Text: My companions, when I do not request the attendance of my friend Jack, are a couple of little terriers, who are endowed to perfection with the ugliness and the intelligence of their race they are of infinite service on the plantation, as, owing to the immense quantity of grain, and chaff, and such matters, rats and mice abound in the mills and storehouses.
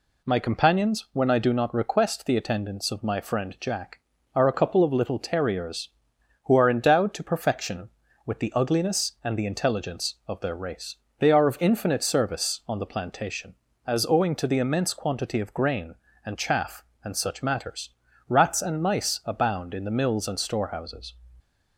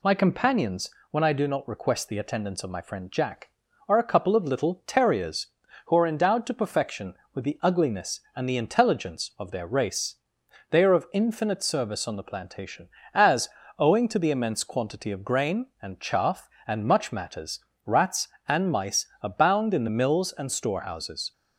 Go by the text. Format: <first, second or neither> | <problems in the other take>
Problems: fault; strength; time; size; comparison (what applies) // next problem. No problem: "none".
first | pauses between "race" and "they"; noticeable; at 10.1 s; 0.54 s long; slight in the first // says "much" for "such"; at 16.8 s // pauses between "mice" and "abound"; slight; at 19.0 s; 0.16 s long